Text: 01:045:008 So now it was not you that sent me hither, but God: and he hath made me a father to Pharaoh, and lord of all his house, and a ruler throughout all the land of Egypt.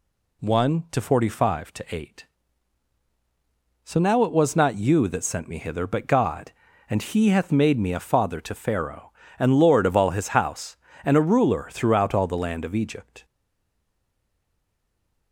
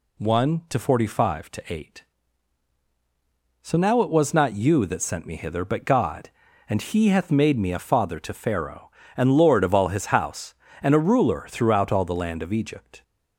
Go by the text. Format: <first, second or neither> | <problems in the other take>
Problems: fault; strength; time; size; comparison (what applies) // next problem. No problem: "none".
second | stays silent after the last word; noticeable; from 13.2 s on; 2.1 s long